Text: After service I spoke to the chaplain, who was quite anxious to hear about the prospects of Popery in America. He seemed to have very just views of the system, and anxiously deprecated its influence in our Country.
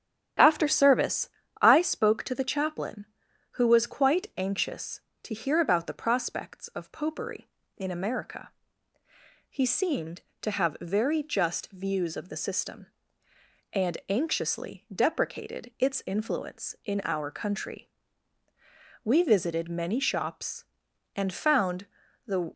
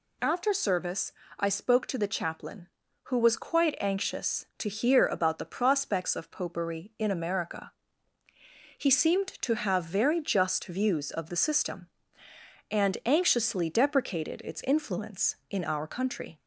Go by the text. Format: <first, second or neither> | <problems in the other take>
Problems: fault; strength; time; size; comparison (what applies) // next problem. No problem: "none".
second | starts louder than the rest; strong; until 1.7 s; 10 dB // pauses between "service" and "I"; slight; at 1.2 s; 0.32 s long; slight in the second // goes on to say "We visited many shops and found the"; strong; from 19.0 s on; 3.5 s long